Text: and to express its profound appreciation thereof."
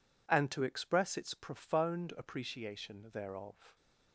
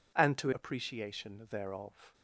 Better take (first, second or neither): first